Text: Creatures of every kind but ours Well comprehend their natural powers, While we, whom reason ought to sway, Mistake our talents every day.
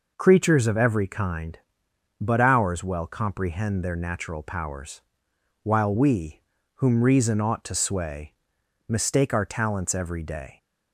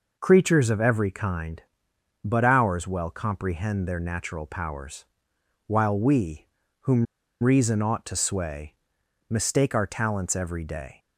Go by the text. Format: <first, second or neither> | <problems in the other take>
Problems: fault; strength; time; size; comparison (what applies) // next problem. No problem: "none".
first | pauses between "whom" and "reason"; at 7.0 s; 0.37 s long